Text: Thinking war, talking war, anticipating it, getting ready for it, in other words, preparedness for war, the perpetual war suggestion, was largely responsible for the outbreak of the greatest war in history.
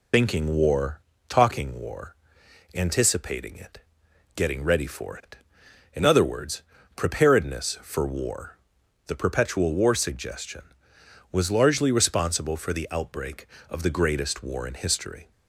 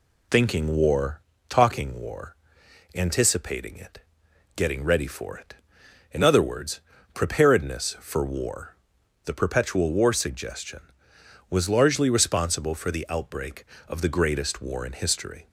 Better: second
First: loses the start of "Thinking"; at 0.1 s; 35 ms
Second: none

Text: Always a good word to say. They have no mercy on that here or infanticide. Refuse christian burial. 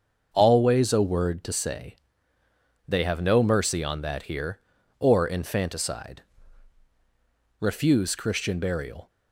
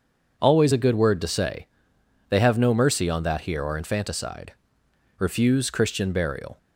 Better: second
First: starts louder than the rest; until 1.3 s; 6.5 dB // skips "good"; at 1.0 s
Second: none

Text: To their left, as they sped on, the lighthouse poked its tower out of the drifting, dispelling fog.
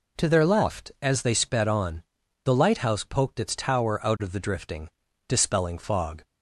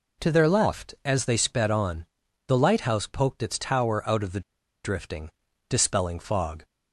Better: first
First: none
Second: pauses between "the" and "drifting"; at 4.3 s; 0.44 s long

